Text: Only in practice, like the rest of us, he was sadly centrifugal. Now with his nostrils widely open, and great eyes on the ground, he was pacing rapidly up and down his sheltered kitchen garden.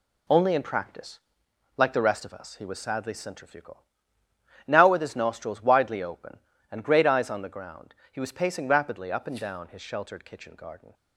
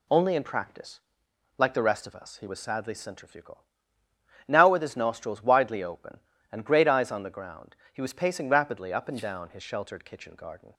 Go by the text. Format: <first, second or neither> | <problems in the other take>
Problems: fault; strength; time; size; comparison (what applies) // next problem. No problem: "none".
second | gets quieter; throughout; 7 dB